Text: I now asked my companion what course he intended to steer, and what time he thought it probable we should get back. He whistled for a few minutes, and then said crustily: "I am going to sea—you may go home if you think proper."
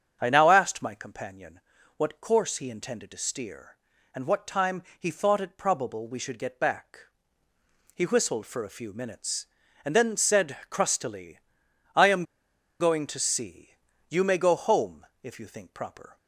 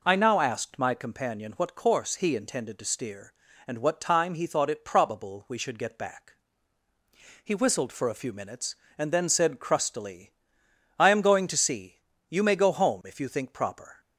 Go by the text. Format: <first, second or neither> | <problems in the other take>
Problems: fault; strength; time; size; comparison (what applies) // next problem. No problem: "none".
second | starts louder than the rest; strong; until 1.2 s; 7 dB // pauses between "companion" and "what"; slight; at 1.6 s; 0.36 s long // pauses between "time" and "he"; slight; at 4.8 s; 0.16 s long // pauses between "am" and "going"; noticeable; at 12.2 s; 0.55 s long // pauses between "home" and "if"; slight; at 15.0 s; 0.16 s long